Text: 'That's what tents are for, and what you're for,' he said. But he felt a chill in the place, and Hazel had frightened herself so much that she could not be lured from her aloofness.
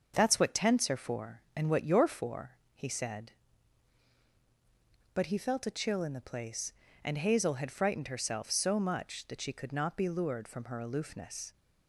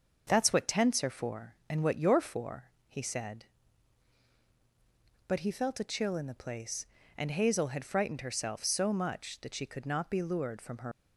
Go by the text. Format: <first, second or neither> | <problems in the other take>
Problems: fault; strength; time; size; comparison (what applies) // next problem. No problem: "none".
first | starts louder than the rest; until 1.2 s; 6.5 dB; also in the first // stops before "aloofness"; at 10.9 s